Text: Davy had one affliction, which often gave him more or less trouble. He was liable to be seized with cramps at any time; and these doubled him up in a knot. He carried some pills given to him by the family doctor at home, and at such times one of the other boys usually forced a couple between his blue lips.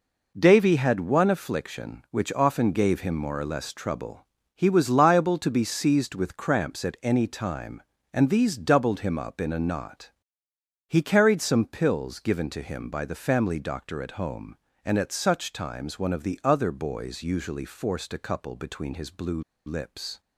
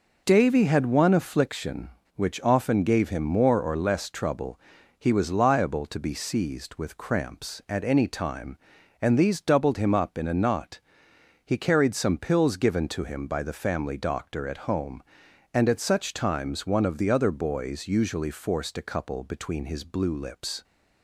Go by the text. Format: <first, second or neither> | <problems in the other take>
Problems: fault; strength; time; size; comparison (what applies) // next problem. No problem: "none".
second | pauses between "blue" and "lips"; slight; at 19.4 s; 0.25 s long